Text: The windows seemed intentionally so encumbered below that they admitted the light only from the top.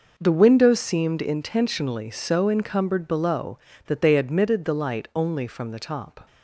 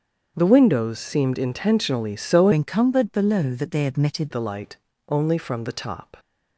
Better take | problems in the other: first | starts louder than the rest; strong; until 1.3 s; 7 dB // changes voice from "encumbered" to "admitted"; from 2.5 to 4.3 s; 1.8 s long // pauses between "light" and "only"; slight; at 4.7 s; 0.30 s long

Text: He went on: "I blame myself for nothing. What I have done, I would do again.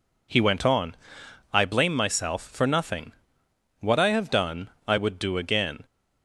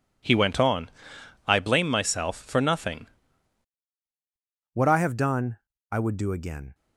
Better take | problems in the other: first | changes voice at "What"; from 4.7 s on; 2.0 s long

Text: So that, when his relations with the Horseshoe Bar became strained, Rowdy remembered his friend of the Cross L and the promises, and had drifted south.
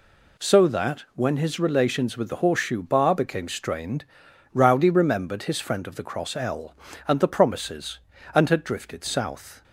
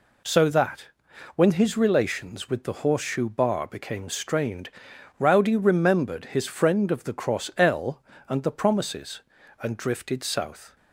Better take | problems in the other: first | skips "had"; at 9.7 s

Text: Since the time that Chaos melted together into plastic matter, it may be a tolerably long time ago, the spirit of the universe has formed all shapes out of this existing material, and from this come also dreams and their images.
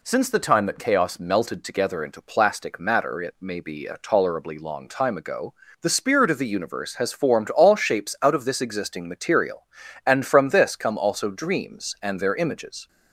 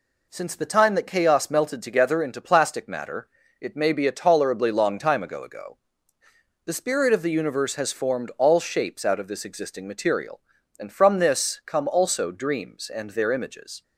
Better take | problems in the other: first | says "ago" twice; at 5.4 s

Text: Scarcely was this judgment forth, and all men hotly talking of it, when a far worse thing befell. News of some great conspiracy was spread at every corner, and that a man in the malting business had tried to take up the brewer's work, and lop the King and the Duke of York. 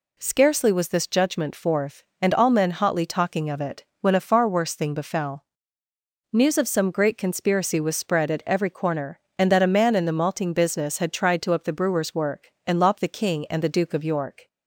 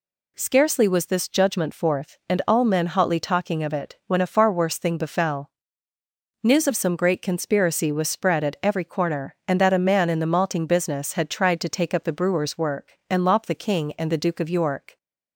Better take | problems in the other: second | skips "take"; at 11.5 s

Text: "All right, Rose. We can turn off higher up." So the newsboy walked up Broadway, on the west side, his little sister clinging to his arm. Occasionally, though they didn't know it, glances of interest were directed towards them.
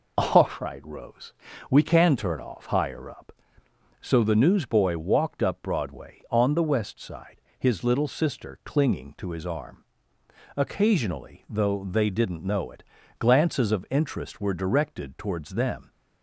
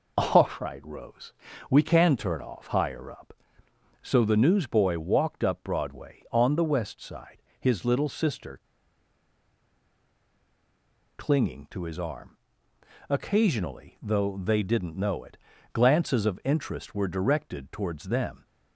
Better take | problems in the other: first | pauses between "sister" and "clinging"; strong; at 8.5 s; 2.5 s long

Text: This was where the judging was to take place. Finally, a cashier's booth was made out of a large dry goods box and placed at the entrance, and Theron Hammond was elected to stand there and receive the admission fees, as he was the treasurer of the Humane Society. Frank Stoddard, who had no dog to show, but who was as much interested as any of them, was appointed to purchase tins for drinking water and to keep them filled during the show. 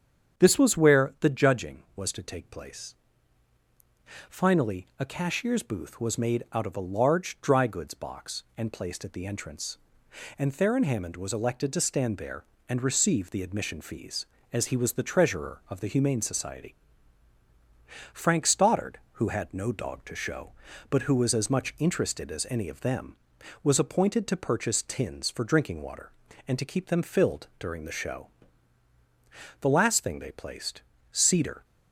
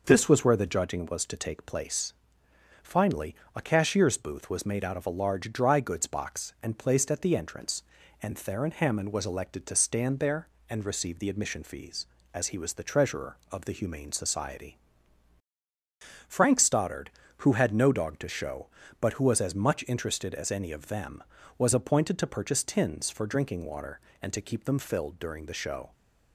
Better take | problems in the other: second | starts louder than the rest; strong; until 1.4 s; 8 dB // goes on to say "The last thing they placed cedar"; strong; from 29.6 s on; 2.0 s long

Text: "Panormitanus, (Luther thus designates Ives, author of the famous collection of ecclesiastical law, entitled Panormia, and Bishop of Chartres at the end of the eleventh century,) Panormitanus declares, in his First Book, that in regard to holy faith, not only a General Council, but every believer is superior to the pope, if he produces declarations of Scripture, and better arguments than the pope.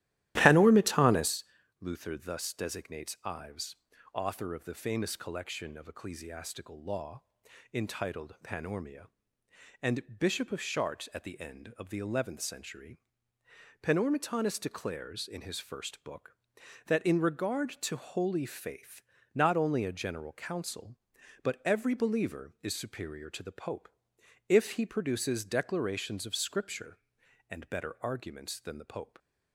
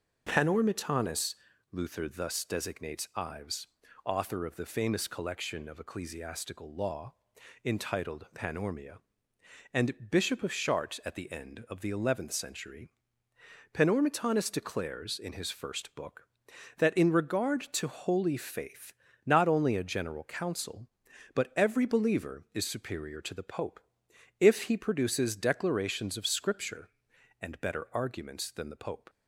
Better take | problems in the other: second | starts louder than the rest; strong; until 1.3 s; 14 dB

